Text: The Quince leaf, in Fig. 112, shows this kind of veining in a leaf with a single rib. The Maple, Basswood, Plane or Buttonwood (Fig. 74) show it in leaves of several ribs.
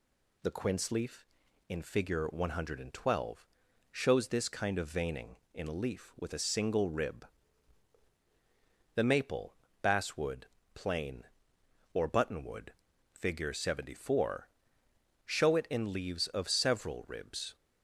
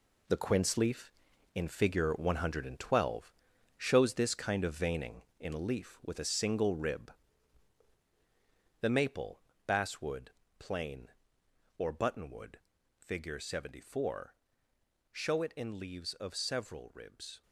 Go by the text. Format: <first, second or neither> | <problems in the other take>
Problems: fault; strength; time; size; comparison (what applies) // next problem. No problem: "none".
first | gets quieter; strong; throughout; 9 dB